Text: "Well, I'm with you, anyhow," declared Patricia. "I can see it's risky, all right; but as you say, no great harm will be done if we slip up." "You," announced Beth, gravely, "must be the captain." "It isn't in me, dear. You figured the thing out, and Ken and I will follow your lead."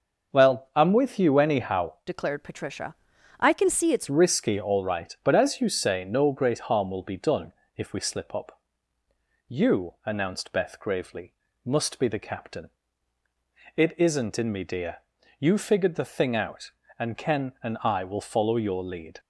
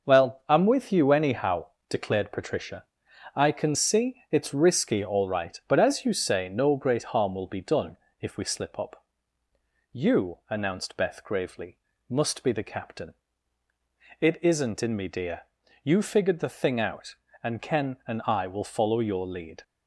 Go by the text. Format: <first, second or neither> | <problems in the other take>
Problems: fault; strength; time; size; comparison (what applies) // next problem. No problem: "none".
second | changes voice from "declared" to "it's"; from 2.0 to 4.0 s; 2.0 s long // pauses between "done" and "if"; slight; at 7.5 s; 0.24 s long; slight in the second